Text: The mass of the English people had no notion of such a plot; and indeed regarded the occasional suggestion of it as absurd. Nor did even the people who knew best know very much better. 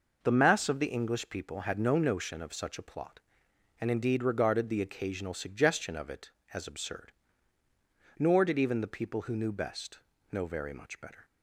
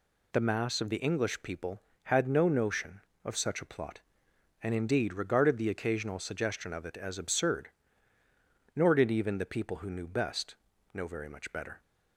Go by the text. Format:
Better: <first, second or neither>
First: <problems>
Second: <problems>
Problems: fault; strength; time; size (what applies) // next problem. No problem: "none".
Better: neither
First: pauses between "best" and "know"; slight; at 9.9 s; 0.32 s long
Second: pauses between "best" and "know"; at 10.5 s; 0.38 s long